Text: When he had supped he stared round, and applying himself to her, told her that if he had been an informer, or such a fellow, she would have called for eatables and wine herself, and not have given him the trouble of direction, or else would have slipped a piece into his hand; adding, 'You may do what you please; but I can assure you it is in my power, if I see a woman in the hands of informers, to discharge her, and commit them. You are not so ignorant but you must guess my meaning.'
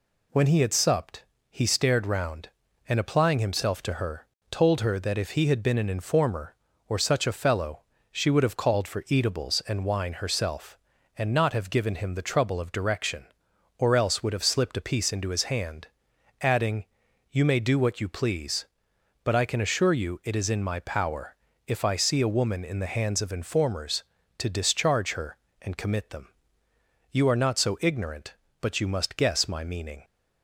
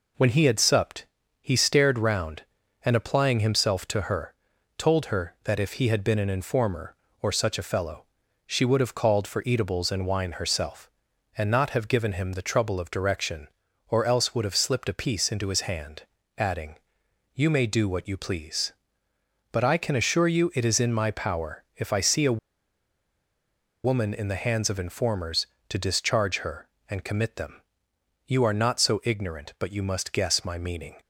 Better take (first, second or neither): first